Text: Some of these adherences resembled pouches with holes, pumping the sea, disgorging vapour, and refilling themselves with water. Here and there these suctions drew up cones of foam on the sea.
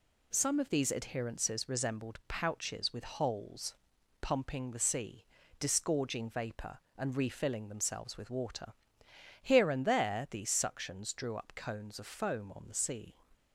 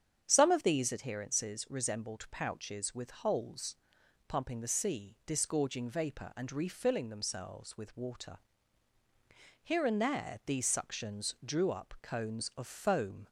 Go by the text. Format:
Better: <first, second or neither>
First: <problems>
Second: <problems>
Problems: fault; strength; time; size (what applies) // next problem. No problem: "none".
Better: first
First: none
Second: starts louder than the rest; strong; until 1.2 s; 8 dB // stops before "on the sea"; at 13.2 s